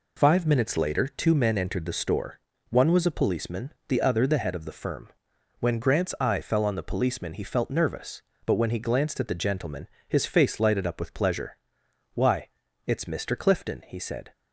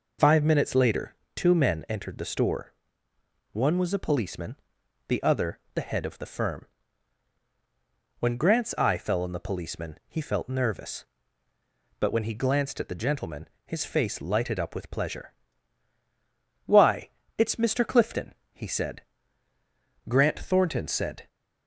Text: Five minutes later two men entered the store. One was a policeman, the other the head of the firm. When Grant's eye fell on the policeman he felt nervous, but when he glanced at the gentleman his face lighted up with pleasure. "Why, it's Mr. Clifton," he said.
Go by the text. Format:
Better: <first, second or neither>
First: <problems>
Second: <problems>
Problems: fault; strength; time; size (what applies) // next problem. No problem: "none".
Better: first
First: pauses between "gentleman" and "his"; slight; at 9.8 s; 0.22 s long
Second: pauses between "later" and "two"; slight; at 1.1 s; 0.18 s long // pauses between "other" and "the"; slight; at 5.5 s; 0.16 s long // pauses between "gentleman" and "his"; slight; at 13.4 s; 0.18 s long // goes on to say "Grant Thornton said"; noticeable; from 20.0 s on; 1.2 s long